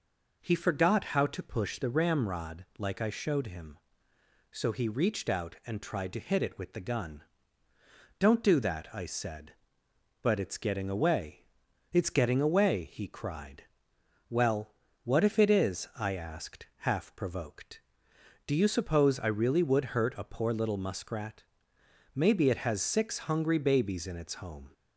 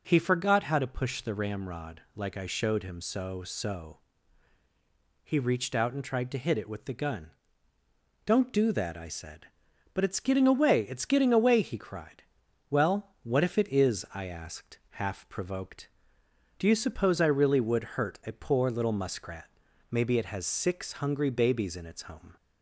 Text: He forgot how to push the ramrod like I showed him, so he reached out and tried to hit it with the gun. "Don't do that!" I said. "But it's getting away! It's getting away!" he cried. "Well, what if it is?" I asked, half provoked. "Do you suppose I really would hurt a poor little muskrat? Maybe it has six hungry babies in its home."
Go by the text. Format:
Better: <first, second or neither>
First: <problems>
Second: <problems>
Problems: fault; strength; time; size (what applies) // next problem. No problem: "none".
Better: first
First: none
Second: says "so" twice; at 3.4 s